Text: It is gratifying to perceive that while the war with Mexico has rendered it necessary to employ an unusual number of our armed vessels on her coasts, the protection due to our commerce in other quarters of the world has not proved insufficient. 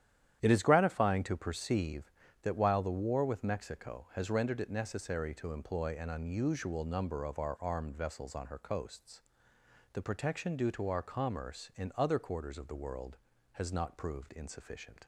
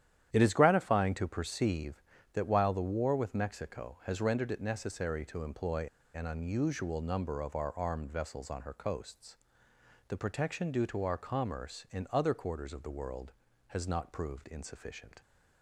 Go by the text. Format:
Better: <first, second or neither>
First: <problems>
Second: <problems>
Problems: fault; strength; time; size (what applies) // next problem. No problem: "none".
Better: first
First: starts louder than the rest; strong; until 1.4 s; 10.5 dB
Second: starts louder than the rest; strong; until 1.3 s; 10.5 dB // pauses between "employ" and "an"; slight; at 5.8 s; 0.27 s long